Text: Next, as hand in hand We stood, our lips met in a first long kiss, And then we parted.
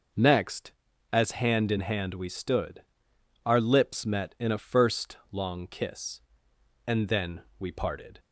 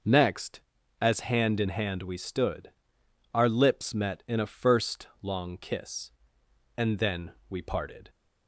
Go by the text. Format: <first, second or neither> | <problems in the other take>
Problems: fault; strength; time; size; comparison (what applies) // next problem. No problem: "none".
neither | pauses between "then" and "we"; slight; the same in both